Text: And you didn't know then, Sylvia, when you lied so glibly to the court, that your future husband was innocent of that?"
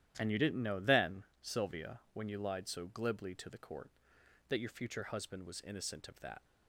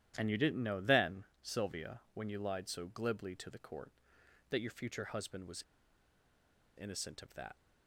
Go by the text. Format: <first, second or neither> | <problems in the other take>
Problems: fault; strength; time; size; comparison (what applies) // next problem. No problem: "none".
first | starts louder than the rest; strong; until 1.1 s; 11.5 dB; strong in the first // pauses between "was" and "innocent"; at 5.6 s; 1.1 s long